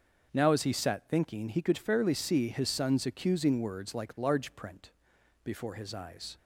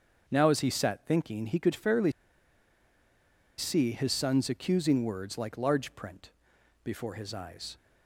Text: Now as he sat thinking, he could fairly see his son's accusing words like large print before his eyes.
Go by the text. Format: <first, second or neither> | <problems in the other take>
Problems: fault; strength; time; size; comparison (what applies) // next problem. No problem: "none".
first | starts louder than the rest; until 1.2 s; 7 dB; also in the first // pauses between "fairly" and "see"; strong; at 2.1 s; 1.4 s long // pauses between "print" and "before"; noticeable; at 6.3 s; 0.52 s long; noticeable in the first